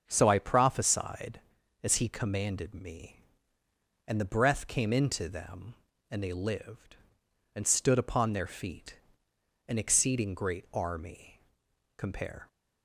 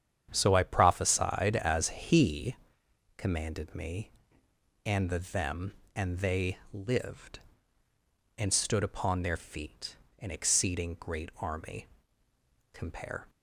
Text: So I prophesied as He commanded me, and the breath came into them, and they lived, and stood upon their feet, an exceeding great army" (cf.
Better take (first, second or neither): first